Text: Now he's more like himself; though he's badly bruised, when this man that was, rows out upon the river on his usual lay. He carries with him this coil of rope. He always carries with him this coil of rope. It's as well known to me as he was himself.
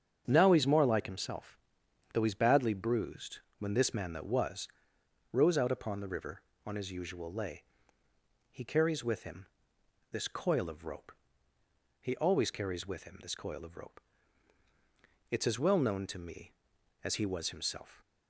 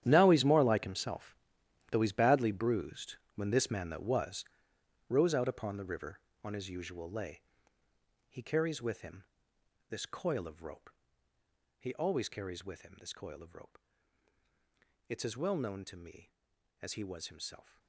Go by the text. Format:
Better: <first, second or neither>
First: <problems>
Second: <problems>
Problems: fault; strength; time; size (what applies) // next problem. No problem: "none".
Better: first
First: starts louder than the rest; until 1.3 s; 7 dB // pauses between "him" and "this"; noticeable; at 9.4 s; 0.68 s long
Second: gets quieter; strong; throughout; 15.5 dB // starts louder than the rest; strong; until 1.0 s; 10 dB // pauses between "him" and "this"; noticeable; at 9.2 s; 0.68 s long